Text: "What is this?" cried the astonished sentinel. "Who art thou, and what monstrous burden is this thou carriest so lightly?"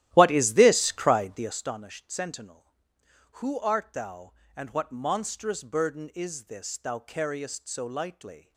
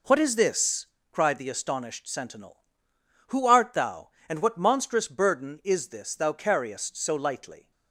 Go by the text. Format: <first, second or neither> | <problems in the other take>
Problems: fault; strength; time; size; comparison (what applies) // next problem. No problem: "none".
second | starts louder than the rest; strong; until 1.6 s; 13.5 dB